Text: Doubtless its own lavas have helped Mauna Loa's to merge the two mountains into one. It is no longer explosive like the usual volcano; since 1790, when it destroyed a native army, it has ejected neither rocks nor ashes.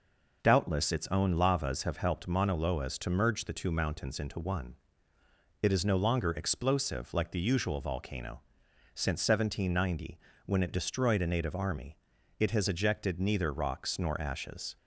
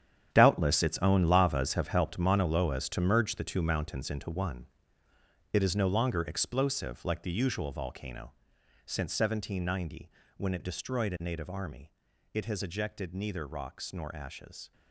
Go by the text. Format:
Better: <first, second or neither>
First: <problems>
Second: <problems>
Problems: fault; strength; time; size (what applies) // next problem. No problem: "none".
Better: first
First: none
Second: gets quieter; strong; throughout; 13 dB